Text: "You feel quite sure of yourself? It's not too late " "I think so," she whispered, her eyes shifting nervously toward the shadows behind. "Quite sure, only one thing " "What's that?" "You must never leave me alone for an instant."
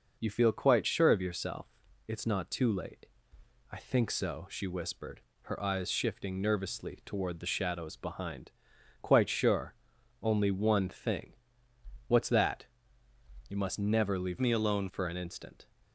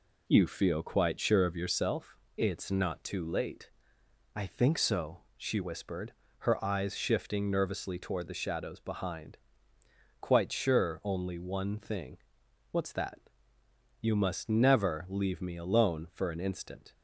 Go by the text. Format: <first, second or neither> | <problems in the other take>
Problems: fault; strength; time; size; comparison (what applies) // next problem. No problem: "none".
second | changes voice from "me" to "alone"; from 14.3 to 14.8 s; 0.5 s long